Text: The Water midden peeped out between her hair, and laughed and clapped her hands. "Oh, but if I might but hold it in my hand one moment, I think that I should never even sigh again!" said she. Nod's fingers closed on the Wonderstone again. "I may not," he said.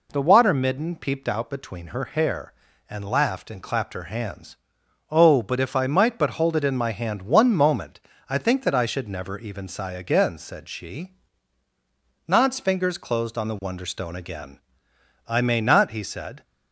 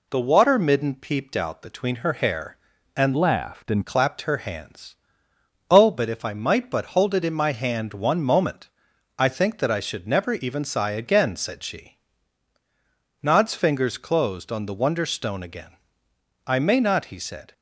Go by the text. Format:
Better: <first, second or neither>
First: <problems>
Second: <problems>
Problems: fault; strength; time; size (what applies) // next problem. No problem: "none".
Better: first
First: none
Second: changes voice from "laughed" to "and"; from 3.1 to 3.8 s; 0.7 s long